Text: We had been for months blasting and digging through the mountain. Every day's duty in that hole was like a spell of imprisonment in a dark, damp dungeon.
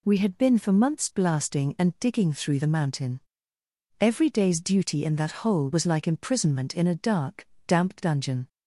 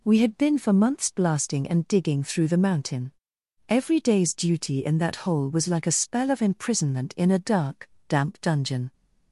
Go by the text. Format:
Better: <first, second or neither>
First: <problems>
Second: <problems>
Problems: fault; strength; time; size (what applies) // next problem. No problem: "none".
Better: second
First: skips "a spell of"; at 6.0 s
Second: none